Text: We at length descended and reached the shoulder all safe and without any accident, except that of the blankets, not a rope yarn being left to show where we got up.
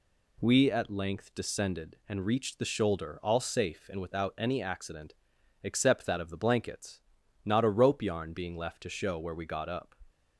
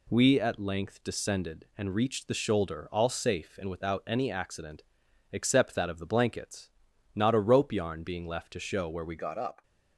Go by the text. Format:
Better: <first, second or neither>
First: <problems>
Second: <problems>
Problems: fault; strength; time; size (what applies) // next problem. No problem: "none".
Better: first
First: none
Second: changes voice at "got"; from 9.1 s on; 0.5 s long